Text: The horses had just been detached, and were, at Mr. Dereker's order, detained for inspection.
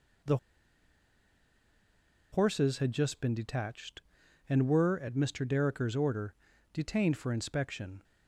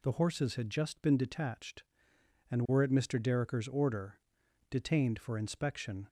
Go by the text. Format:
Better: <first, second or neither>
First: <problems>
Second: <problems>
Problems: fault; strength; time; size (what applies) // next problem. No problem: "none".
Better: second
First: pauses between "The" and "horses"; strong; at 0.3 s; 1.9 s long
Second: none